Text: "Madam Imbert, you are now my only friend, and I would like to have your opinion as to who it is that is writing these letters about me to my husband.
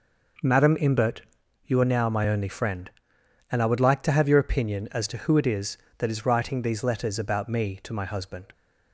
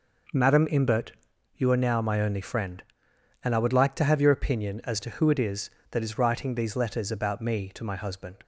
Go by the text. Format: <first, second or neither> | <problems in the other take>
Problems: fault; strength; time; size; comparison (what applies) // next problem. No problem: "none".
neither | none